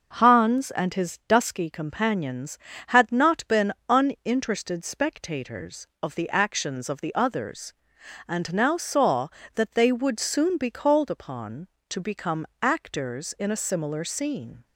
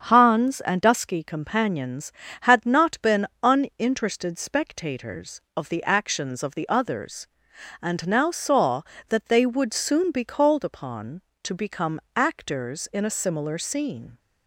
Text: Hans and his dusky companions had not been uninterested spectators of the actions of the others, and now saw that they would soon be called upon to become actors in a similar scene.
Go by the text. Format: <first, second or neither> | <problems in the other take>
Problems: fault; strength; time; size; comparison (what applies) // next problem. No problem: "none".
first | starts louder than the rest; strong; until 1.0 s; 7.5 dB // skips "his"; at 0.8 s // pauses between "been" and "uninterested"; slight; at 3.2 s; 0.18 s long; slight in the first // pauses between "become" and "actors"; slight; at 11.9 s; 0.16 s long; slight in the first